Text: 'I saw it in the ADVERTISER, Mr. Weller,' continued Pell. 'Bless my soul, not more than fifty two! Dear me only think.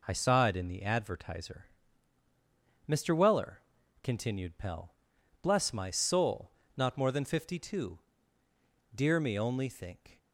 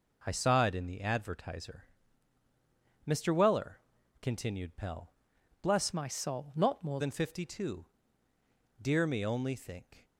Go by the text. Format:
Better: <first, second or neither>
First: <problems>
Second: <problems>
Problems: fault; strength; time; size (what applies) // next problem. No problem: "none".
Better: first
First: none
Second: changes voice from "my" to "more"; from 5.9 to 7.0 s; 1.1 s long